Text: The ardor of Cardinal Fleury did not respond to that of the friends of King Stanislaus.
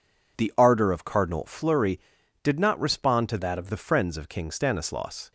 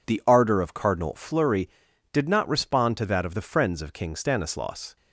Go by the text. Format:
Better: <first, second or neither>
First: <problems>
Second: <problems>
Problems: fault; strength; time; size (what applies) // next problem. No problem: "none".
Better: second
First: changes voice from "that" to "of"; from 3.3 to 3.6 s; 0.3 s long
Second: none